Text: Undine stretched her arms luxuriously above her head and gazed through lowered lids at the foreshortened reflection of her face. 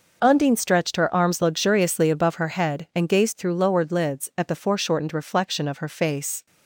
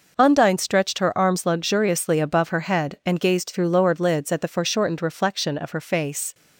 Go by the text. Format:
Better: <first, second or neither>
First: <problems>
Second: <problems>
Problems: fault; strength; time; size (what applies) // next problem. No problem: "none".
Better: neither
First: none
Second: none